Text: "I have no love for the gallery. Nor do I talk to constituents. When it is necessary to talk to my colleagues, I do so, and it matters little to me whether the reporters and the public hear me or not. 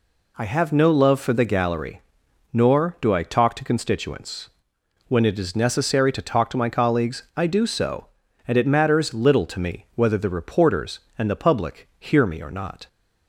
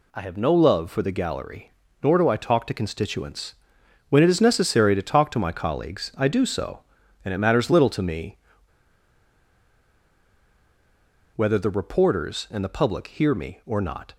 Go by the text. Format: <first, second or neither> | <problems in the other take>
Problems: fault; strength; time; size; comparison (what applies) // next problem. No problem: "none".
first | pauses between "me" and "whether"; strong; at 8.3 s; 2.9 s long